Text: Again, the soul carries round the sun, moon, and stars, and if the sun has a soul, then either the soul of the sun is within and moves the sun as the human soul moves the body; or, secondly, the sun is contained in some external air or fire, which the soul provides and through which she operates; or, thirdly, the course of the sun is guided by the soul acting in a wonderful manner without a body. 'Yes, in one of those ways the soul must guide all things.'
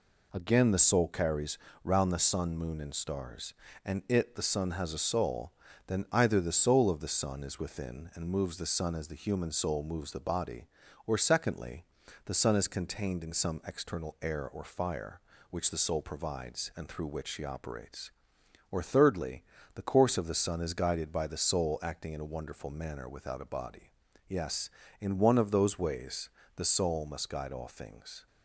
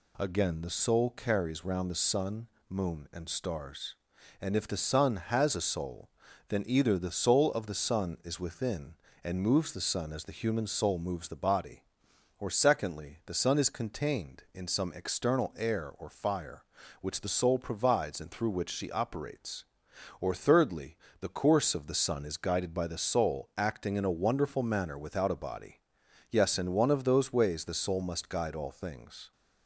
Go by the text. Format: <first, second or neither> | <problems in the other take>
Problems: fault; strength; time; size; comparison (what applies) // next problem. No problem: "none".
second | pauses between "carries" and "round"; slight; at 1.5 s; 0.26 s long // says "it" for "if"; at 4.0 s // pauses between "ways" and "the"; slight; at 26.3 s; 0.26 s long